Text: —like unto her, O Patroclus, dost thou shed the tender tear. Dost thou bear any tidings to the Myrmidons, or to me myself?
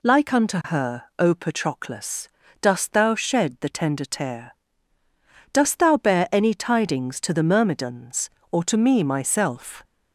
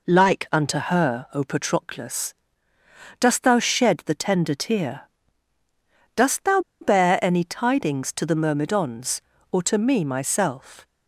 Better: first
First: none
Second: pauses between "thou" and "bear"; slight; at 6.5 s; 0.21 s long

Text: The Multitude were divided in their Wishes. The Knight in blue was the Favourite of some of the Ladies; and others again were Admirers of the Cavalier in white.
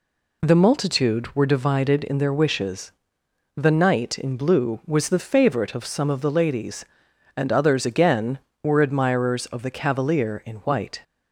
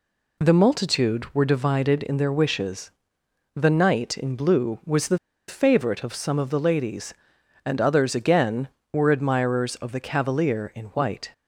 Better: first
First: none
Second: pauses between "the" and "Favourite"; slight; at 5.1 s; 0.30 s long

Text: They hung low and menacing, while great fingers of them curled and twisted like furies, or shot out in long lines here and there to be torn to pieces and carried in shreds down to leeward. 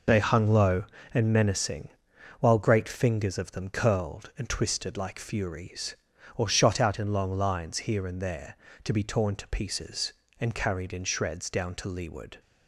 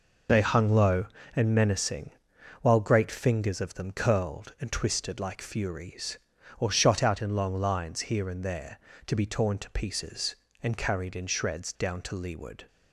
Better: neither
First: none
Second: none

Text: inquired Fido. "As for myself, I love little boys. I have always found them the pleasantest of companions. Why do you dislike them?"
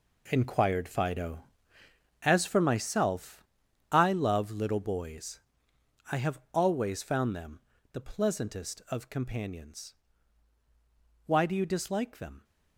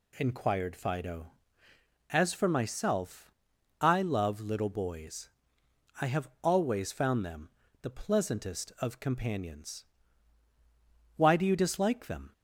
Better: second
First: gets quieter; strong; throughout; 10.5 dB // pauses between "them" and "the"; slight; at 7.6 s; 0.32 s long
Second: pauses between "them" and "the"; slight; at 7.4 s; 0.32 s long

